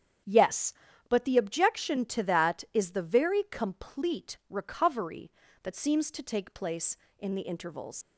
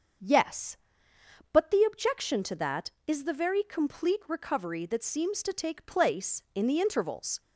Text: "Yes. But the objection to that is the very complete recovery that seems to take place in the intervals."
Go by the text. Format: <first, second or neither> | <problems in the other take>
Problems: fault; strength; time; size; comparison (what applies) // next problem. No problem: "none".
second | starts louder than the rest; strong; until 1.6 s; 9 dB; also in the second // leaves "intervals" unfinished; at 8.0 s; 80 ms